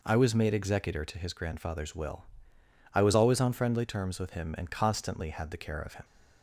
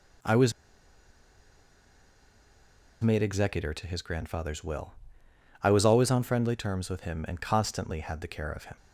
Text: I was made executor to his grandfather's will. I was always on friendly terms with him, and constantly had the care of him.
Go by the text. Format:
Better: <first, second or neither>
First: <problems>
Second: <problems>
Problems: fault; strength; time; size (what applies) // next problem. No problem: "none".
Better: first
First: none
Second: pauses between "was" and "made"; strong; at 0.5 s; 2.4 s long